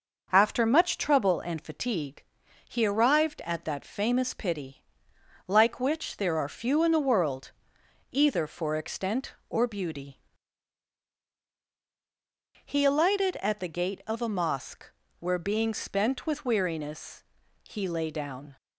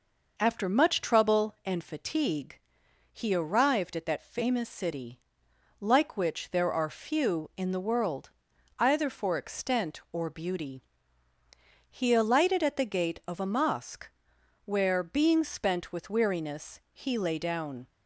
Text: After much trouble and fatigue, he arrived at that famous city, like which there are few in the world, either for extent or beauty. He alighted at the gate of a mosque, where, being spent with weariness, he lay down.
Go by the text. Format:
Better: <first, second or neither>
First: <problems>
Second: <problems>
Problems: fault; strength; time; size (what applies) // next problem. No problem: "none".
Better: second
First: starts louder than the rest; noticeable; until 1.3 s; 6 dB // says "pity" for "city"; at 4.3 s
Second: none